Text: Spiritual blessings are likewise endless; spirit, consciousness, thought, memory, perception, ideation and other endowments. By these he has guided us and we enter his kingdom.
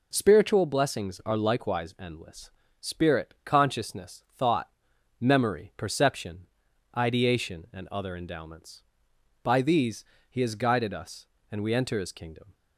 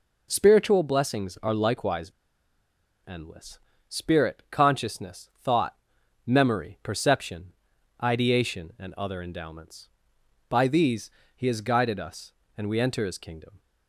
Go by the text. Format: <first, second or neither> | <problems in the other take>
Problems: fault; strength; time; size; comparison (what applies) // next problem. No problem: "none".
first | pauses between "likewise" and "endless"; noticeable; at 2.1 s; 0.95 s long // pauses between "these" and "he"; slight; at 11.1 s; 0.26 s long; slight in the first